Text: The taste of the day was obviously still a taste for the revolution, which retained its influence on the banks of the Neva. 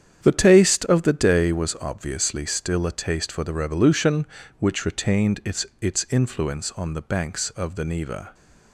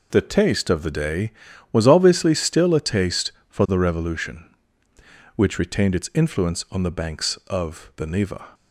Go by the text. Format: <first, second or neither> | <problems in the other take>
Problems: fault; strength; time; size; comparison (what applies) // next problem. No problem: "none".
second | starts louder than the rest; strong; until 1.2 s; 8.5 dB // says "its" twice; at 5.8 s